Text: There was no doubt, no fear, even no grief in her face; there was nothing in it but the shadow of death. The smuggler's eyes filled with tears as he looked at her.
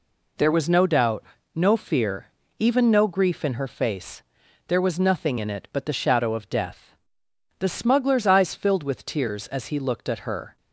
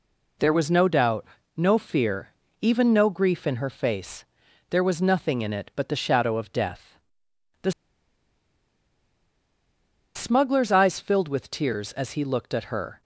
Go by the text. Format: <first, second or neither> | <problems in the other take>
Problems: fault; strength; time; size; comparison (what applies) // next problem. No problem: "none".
first | pauses between "The" and "smuggler's"; strong; at 7.7 s; 2.4 s long